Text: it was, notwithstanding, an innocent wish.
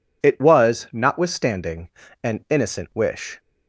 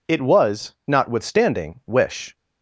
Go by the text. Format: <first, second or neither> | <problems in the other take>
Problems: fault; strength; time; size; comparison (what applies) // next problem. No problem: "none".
first | skips "an innocent"; at 1.8 s